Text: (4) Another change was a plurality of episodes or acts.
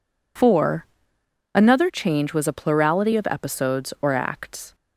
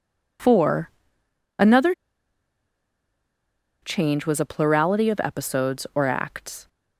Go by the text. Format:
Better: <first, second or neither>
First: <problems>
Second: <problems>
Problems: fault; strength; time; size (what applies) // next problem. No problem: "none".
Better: first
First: none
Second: pauses between "Another" and "change"; strong; at 1.9 s; 1.8 s long